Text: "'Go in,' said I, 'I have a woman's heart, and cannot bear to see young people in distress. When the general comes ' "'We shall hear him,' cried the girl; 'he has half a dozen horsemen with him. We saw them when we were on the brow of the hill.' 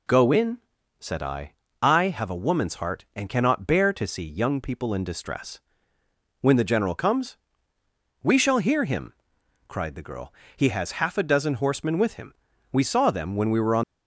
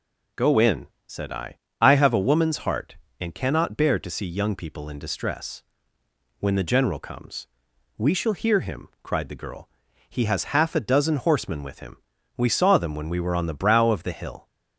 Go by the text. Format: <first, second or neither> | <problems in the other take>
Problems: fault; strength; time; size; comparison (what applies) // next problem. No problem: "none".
second | stops before "the brow of the hill"; at 13.8 s